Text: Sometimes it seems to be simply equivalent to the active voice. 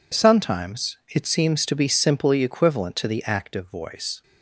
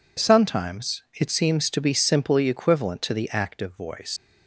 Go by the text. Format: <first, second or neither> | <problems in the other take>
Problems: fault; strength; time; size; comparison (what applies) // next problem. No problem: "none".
first | leaves "voice" unfinished; at 4.1 s; 120 ms